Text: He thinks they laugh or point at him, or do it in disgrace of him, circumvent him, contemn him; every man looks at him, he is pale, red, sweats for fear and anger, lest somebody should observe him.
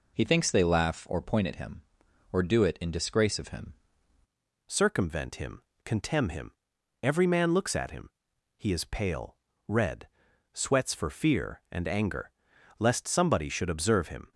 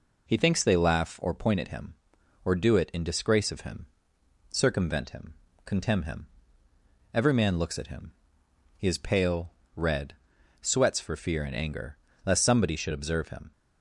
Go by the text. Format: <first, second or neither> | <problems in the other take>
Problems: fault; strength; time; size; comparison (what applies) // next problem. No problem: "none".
second | changes voice at "circumvent"; from 4.6 s on; 9.7 s long